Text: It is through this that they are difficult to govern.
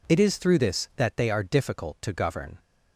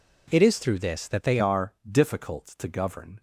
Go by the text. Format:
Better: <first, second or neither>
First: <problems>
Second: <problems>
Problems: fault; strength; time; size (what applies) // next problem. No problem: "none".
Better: first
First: none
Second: changes voice at "are"; from 1.3 s on; 1.9 s long